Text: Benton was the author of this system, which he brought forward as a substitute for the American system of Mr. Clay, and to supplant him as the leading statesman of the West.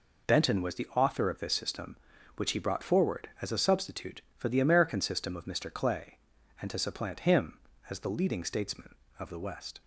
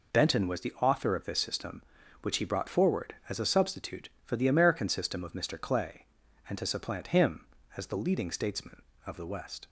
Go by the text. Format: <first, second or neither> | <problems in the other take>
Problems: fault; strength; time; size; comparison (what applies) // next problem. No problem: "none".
neither | none